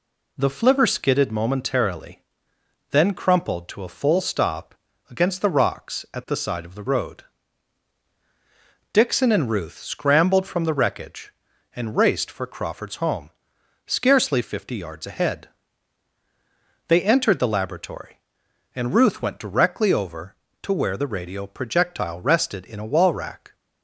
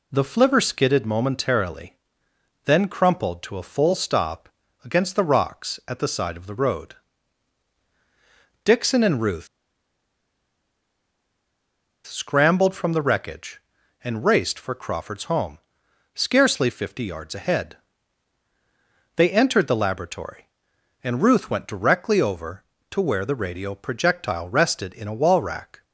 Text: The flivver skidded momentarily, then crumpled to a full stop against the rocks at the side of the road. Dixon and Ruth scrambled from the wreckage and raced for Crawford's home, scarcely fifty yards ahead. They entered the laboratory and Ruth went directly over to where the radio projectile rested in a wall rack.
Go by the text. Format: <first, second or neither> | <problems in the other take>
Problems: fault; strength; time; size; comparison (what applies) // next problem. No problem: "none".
first | pauses between "stop" and "against"; slight; at 4.4 s; 0.36 s long; slight in the first // pauses between "Ruth" and "scrambled"; strong; at 9.4 s; 2.5 s long